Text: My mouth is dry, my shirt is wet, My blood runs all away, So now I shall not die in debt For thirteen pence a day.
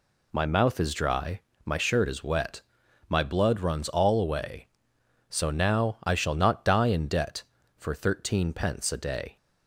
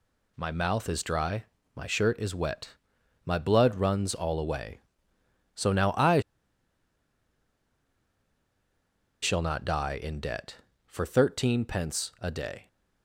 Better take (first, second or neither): first